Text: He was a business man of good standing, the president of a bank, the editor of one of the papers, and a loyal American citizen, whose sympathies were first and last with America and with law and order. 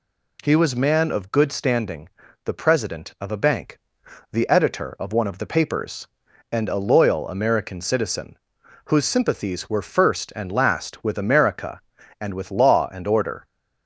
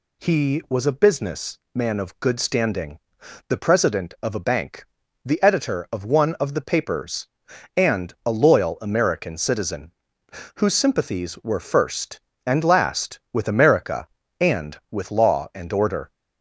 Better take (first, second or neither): second